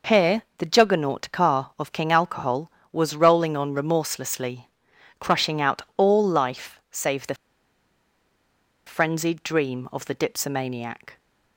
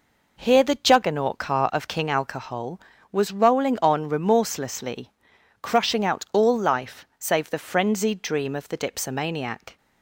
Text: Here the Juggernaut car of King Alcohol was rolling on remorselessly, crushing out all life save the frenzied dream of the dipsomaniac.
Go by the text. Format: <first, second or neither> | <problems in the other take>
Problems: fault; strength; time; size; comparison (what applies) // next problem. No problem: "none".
second | pauses between "Here" and "the"; slight; at 0.4 s; 0.16 s long // pauses between "out" and "all"; slight; at 5.8 s; 0.16 s long // pauses between "the" and "frenzied"; strong; at 7.3 s; 1.5 s long